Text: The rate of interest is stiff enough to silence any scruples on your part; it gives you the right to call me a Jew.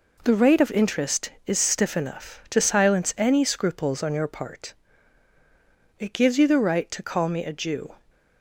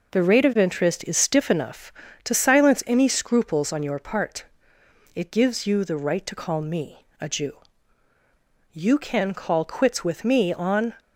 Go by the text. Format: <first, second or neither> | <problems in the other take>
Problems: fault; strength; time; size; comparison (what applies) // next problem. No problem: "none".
first | goes on to say "You can call quits with me on"; strong; from 8.7 s on; 2.2 s long